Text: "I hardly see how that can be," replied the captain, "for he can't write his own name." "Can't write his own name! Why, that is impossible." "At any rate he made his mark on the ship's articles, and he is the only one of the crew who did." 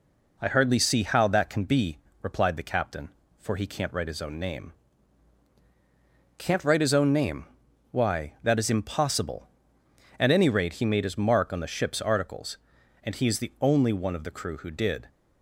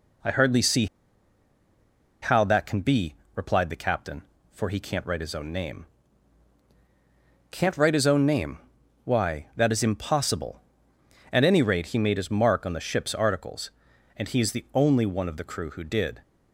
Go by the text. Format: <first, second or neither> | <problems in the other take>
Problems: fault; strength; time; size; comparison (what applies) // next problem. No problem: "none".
first | pauses between "see" and "how"; strong; at 0.8 s; 1.3 s long